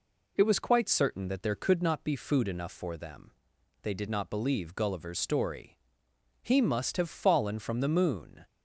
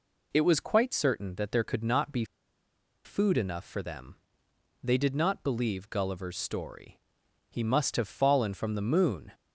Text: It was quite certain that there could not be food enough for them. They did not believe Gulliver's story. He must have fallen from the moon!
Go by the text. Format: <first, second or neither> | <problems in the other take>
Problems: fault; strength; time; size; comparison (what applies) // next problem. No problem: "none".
first | pauses between "be" and "food"; noticeable; at 2.2 s; 0.80 s long